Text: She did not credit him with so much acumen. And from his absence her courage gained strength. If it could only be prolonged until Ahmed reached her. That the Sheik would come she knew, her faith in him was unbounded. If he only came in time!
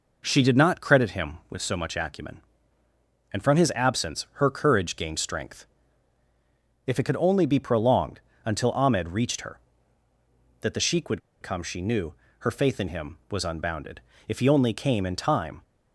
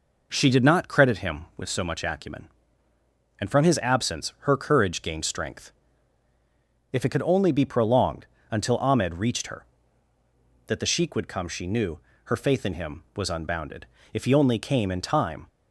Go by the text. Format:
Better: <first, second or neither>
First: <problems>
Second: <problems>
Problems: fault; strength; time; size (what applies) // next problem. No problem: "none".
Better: second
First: pauses between "prolonged" and "until"; slight; at 8.1 s; 0.26 s long // pauses between "would" and "come"; slight; at 11.2 s; 0.22 s long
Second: pauses between "prolonged" and "until"; slight; at 8.2 s; 0.26 s long